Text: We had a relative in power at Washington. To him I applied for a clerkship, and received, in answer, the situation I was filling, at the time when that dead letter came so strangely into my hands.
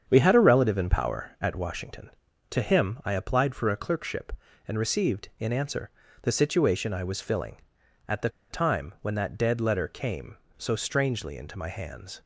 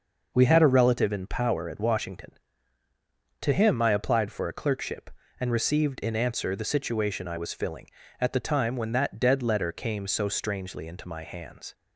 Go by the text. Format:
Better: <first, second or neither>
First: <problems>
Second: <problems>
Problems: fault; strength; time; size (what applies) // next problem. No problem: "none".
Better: second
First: starts louder than the rest; strong; until 1.0 s; 7.5 dB // pauses between "the" and "time"; slight; at 8.2 s; 0.21 s long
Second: none